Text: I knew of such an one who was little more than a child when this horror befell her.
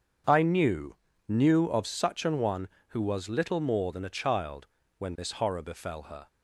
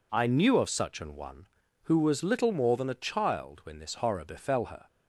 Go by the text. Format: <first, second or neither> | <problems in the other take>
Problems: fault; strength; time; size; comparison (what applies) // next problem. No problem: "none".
second | starts louder than the rest; until 1.6 s; 7 dB // says "knew" twice; at 1.2 s // pauses between "child" and "when"; slight; at 4.6 s; 0.32 s long